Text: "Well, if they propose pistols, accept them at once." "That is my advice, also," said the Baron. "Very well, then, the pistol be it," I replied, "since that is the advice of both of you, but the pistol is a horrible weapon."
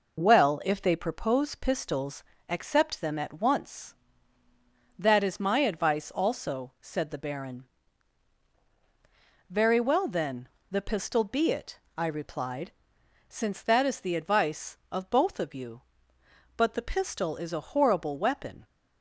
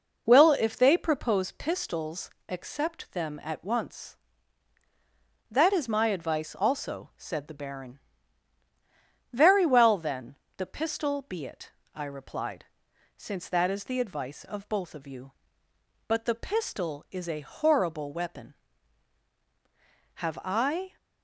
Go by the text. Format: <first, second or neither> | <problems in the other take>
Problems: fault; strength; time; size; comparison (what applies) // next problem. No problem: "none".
first | goes on to say "Have I"; noticeable; from 20.1 s on; 0.82 s long